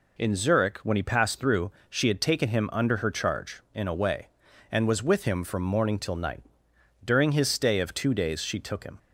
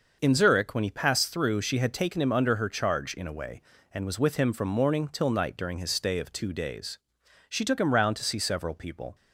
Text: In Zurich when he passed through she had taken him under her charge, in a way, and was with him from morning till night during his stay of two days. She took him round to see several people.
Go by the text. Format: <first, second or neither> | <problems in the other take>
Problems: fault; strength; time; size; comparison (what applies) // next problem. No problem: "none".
second | pauses between "through" and "she"; slight; at 1.7 s; 0.20 s long // pauses between "night" and "during"; noticeable; at 6.4 s; 0.62 s long // stops before "round to see several people"; at 8.9 s